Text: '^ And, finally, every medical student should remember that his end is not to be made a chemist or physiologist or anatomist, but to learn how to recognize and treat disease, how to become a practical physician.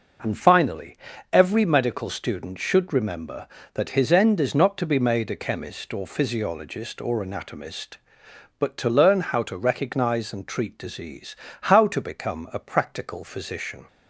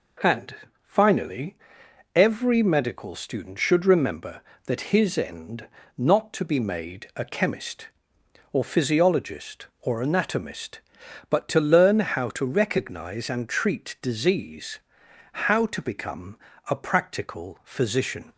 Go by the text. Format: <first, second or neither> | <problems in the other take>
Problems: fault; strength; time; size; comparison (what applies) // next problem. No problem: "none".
first | skips "is"; at 5.8 s // pauses between "become" and "a"; slight; at 16.3 s; 0.32 s long